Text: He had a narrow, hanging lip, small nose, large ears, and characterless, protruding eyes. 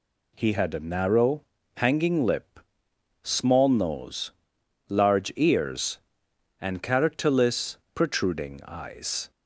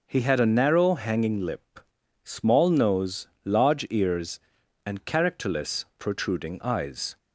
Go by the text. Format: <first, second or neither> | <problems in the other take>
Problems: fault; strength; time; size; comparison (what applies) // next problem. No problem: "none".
neither | none